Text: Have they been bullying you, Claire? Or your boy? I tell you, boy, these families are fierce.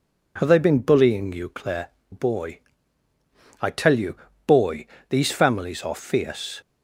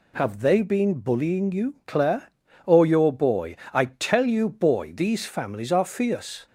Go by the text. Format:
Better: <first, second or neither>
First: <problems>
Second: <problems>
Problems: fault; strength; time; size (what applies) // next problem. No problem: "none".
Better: second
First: skips "Or your"; at 2.0 s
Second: none